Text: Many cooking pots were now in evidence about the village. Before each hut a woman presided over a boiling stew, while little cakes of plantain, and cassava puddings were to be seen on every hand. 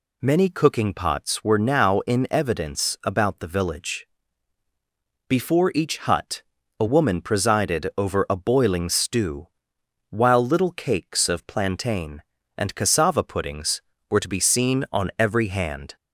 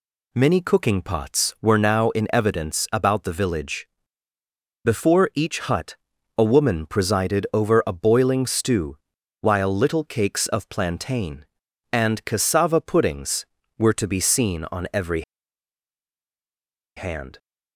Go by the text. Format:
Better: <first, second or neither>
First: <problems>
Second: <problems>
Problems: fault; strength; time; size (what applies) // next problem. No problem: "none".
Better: first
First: pauses between "hut" and "a"; at 6.4 s; 0.38 s long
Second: pauses between "hut" and "a"; at 5.9 s; 0.42 s long // pauses between "every" and "hand"; strong; at 15.2 s; 1.7 s long